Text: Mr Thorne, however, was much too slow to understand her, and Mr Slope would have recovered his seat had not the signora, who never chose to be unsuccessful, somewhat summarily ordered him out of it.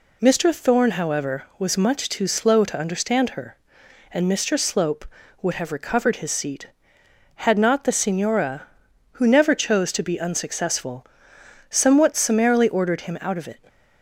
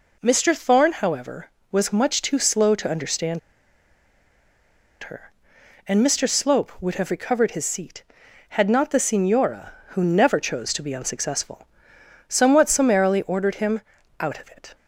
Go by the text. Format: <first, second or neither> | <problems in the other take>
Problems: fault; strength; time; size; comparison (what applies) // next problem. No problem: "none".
first | pauses between "understand" and "her"; strong; at 3.3 s; 1.6 s long // pauses between "him" and "out"; at 13.7 s; 0.40 s long